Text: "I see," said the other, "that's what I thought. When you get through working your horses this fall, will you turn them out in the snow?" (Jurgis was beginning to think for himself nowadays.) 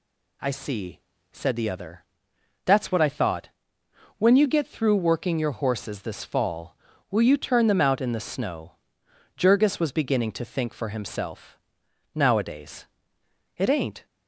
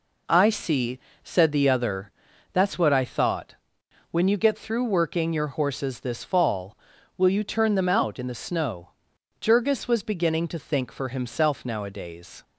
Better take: second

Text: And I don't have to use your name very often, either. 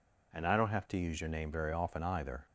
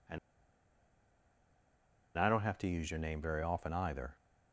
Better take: first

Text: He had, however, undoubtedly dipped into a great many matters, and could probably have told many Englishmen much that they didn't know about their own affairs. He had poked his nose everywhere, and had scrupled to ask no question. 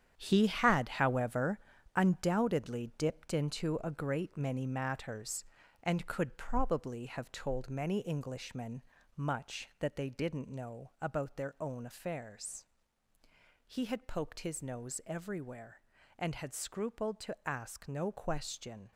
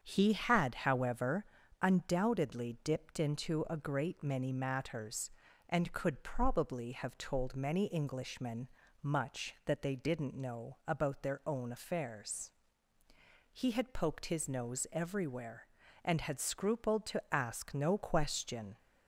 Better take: second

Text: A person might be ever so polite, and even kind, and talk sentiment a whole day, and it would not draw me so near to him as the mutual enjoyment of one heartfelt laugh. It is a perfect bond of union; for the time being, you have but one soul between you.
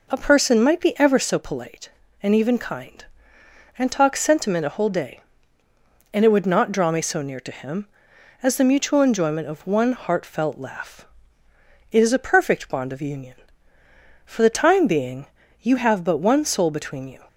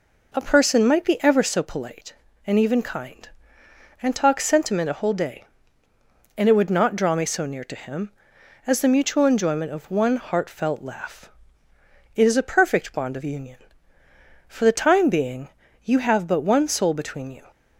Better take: neither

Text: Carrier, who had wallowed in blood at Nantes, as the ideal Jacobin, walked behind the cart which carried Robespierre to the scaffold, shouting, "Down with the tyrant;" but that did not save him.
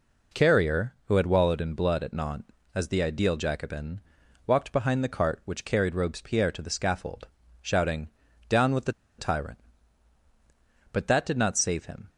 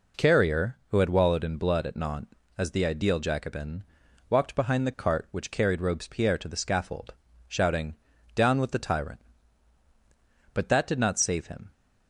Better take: second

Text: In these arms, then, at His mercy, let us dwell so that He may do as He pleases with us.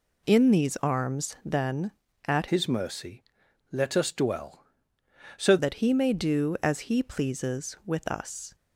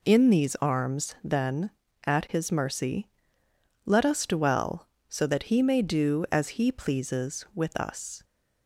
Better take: second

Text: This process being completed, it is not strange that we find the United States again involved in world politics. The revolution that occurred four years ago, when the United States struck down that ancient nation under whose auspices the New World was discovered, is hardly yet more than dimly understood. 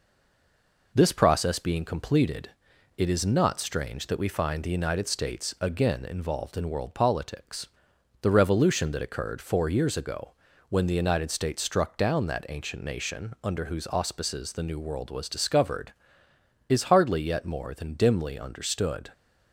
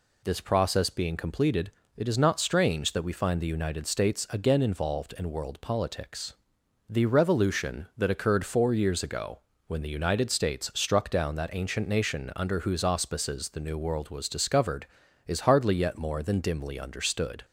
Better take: second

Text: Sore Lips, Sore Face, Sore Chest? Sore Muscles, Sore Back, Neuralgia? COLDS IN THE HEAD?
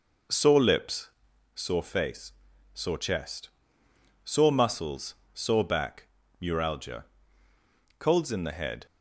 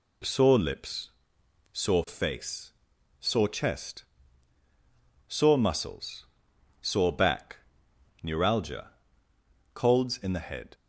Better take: second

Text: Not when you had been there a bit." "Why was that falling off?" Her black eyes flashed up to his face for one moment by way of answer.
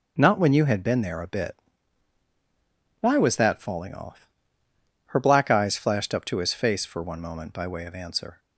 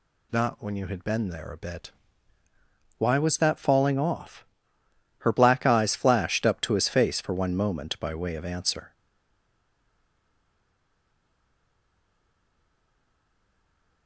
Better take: first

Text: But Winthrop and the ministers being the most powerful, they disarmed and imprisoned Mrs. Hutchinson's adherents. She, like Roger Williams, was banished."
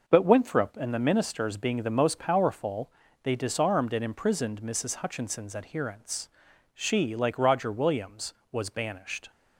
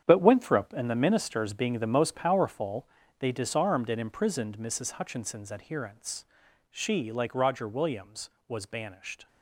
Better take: first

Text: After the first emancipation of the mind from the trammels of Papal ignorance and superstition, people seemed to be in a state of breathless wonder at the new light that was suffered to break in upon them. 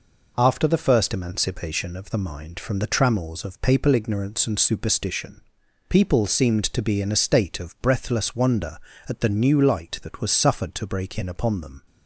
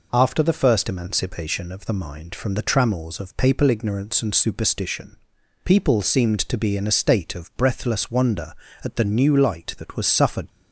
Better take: first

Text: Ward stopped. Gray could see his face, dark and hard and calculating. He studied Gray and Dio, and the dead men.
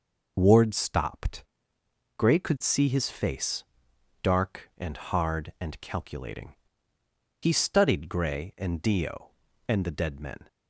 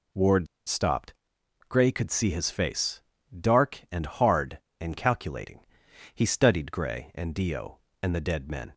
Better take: first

